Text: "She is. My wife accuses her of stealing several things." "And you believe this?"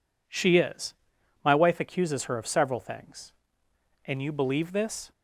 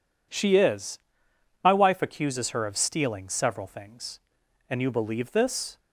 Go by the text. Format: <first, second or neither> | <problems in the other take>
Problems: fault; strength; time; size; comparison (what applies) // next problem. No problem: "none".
second | skips "stealing"; at 2.4 s